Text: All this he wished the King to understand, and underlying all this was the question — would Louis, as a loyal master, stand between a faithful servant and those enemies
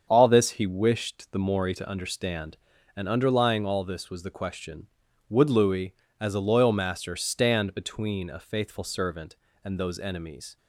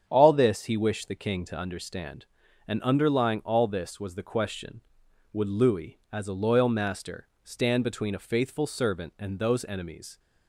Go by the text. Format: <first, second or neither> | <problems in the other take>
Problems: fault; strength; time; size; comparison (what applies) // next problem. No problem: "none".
second | starts louder than the rest; strong; until 1.1 s; 7 dB; strong in the second // says "Mori" for "King"; at 1.3 s